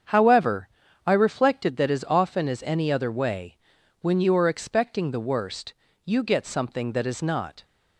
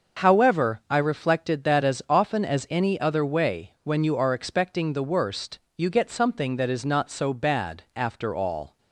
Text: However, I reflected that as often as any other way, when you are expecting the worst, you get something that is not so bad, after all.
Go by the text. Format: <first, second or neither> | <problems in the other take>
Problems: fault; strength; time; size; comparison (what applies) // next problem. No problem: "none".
second | starts louder than the rest; strong; until 1.4 s; 7.5 dB; also in the second // stops before "so bad after all"; at 7.6 s